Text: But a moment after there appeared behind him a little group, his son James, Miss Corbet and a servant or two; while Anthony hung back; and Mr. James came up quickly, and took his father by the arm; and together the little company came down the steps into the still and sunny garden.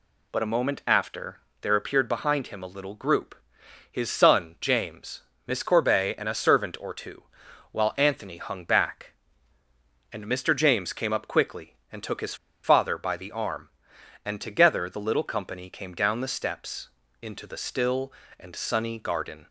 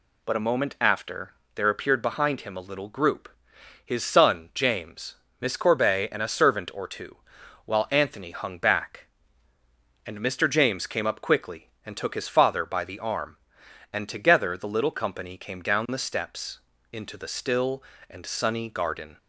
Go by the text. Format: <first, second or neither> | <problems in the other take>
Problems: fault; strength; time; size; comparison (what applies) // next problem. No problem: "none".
second | pauses between "after" and "there"; slight; at 1.3 s; 0.22 s long; slight in the second // pauses between "his" and "father"; slight; at 12.3 s; 0.28 s long // pauses between "steps" and "into"; slight; at 16.8 s; 0.34 s long; slight in the second